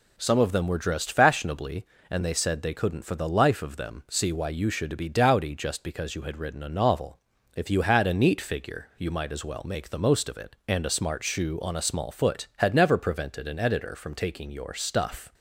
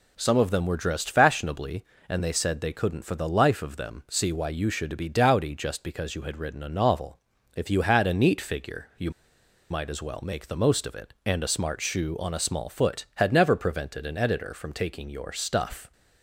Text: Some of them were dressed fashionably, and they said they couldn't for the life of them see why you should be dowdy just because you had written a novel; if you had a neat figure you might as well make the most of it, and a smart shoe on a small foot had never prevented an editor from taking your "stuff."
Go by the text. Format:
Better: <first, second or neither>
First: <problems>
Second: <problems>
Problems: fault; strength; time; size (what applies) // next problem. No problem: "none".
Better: first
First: none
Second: pauses between "you" and "might"; noticeable; at 9.1 s; 0.60 s long